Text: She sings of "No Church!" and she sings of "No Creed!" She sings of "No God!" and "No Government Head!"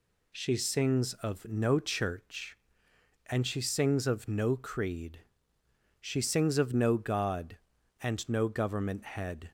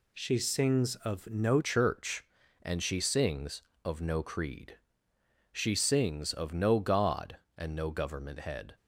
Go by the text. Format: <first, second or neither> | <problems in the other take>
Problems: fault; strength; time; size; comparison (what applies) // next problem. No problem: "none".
first | changes voice at "Church"; from 1.6 s on; 7.1 s long